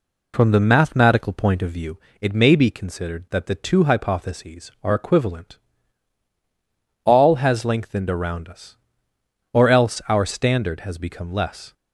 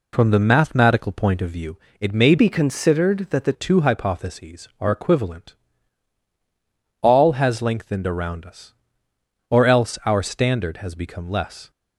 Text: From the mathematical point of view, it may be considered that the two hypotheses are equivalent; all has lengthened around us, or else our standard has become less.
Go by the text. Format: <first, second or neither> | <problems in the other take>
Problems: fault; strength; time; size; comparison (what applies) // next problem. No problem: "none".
first | changes voice from "be" to "the"; from 2.3 to 3.5 s; 1.2 s long